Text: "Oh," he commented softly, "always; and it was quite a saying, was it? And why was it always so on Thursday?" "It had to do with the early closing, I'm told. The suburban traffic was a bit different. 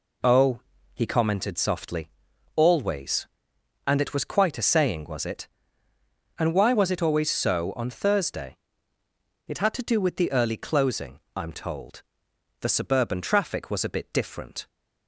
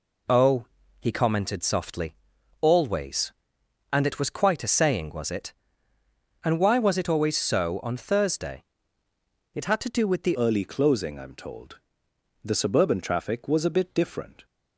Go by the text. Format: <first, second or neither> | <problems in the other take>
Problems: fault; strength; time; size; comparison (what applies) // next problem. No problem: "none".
first | changes voice at "early"; from 10.3 s on; 4.1 s long